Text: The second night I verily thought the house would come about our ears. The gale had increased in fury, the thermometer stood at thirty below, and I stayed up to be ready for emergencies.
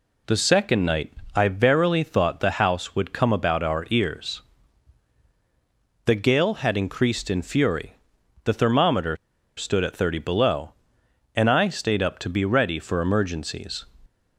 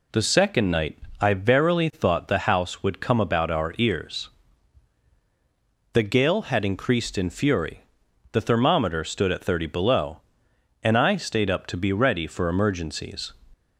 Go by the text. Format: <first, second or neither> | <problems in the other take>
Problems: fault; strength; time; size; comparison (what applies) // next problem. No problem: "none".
second | pauses between "night" and "I"; slight; at 1.1 s; 0.22 s long; slight in the second // pauses between "thermometer" and "stood"; at 9.1 s; 0.40 s long